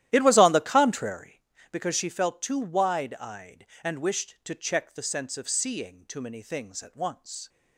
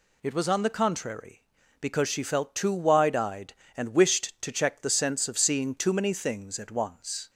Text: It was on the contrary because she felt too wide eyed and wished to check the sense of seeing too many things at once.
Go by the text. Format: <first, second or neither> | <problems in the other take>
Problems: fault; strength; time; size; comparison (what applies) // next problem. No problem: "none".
second | starts louder than the rest; strong; until 1.4 s; 13 dB